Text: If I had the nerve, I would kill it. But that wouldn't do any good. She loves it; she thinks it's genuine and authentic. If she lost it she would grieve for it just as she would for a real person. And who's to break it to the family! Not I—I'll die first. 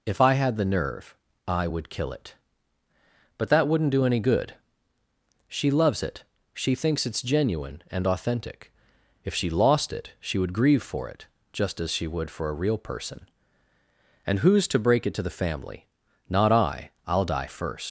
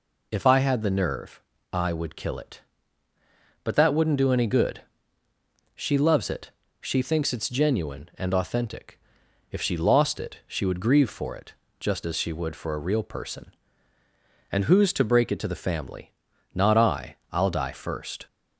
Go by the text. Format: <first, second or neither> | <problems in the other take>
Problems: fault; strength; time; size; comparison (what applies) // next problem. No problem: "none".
second | pauses between "it" and "just"; slight; at 11.2 s; 0.26 s long; slight in the second // leaves "first" unfinished; at 17.8 s; 110 ms